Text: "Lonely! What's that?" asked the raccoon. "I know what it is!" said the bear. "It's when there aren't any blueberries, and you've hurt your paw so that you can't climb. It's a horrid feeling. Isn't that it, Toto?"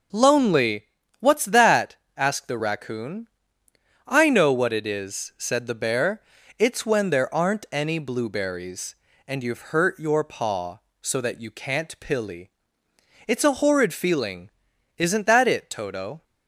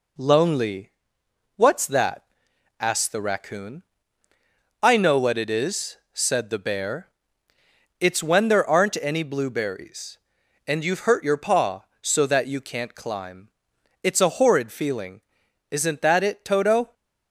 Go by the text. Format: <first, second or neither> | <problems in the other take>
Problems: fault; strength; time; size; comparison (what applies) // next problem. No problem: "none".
second | says "pilly" for "climb"; at 11.9 s